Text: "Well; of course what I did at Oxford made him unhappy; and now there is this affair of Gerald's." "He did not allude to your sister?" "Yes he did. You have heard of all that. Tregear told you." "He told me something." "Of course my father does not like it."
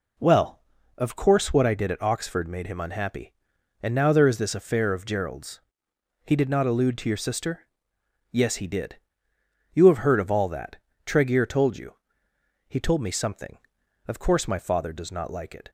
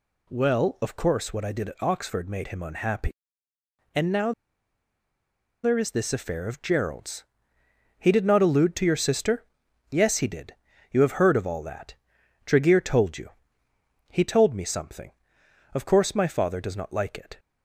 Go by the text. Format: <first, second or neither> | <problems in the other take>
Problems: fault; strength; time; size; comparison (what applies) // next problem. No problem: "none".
first | pauses between "now" and "there"; strong; at 4.3 s; 1.3 s long